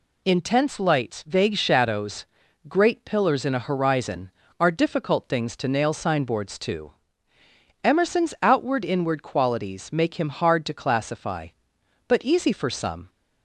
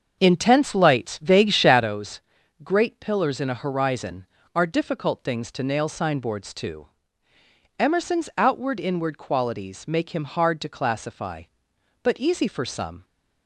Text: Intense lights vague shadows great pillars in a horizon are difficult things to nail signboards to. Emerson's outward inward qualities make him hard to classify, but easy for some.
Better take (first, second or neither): first